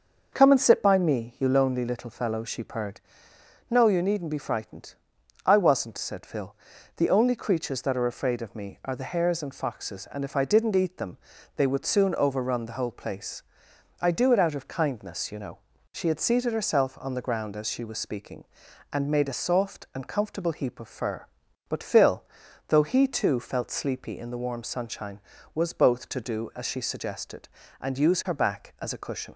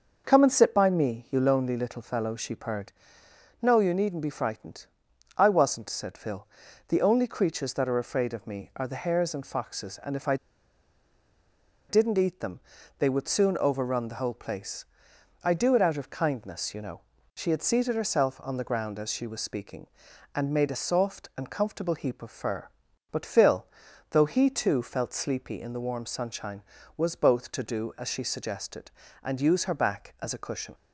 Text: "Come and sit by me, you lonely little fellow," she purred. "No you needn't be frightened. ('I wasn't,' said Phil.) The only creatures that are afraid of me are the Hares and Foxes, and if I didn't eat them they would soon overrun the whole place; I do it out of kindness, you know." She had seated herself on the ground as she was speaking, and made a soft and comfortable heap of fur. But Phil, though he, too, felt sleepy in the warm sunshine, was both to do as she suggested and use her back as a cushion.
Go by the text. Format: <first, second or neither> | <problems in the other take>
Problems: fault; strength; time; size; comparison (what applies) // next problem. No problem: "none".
first | starts louder than the rest; noticeable; until 1.2 s; 6 dB; noticeable in the first // pauses between "I" and "didn't"; strong; at 10.3 s; 1.5 s long // pauses between "them" and "they"; at 12.6 s; 0.38 s long; also in the first